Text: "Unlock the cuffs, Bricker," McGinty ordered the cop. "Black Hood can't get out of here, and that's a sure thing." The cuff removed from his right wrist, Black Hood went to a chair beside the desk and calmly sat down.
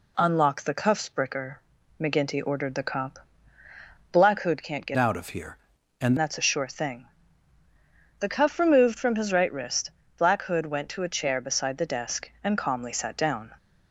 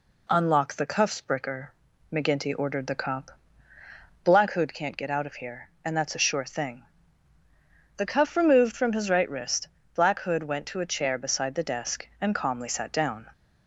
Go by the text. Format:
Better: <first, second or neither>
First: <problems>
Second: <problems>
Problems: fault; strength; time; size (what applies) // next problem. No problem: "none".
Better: second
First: changes voice from "out" to "and"; from 4.9 to 6.1 s; 1.2 s long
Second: none